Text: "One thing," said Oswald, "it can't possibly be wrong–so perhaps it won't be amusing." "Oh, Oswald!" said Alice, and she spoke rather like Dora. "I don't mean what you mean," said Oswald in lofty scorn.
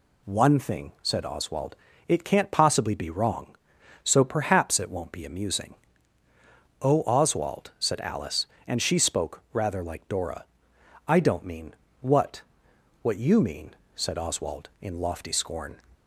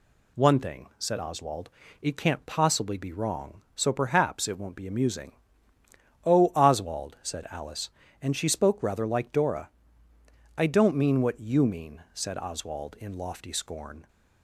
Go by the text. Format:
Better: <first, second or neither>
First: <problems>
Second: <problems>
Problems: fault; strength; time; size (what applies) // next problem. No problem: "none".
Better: second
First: pauses between "mean" and "what"; slight; at 11.7 s; 0.26 s long // says "what" twice; at 13.0 s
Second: none